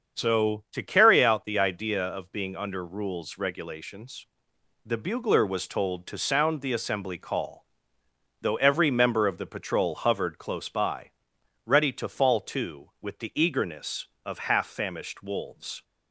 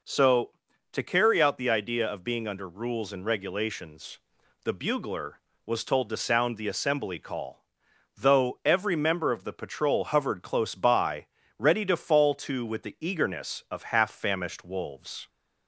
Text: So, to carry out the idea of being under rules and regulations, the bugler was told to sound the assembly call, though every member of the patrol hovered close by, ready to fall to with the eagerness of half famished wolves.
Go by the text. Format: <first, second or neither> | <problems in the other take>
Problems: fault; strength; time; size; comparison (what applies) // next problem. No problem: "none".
second | starts louder than the rest; until 1.2 s; 6.5 dB // skips "and"; at 3.3 s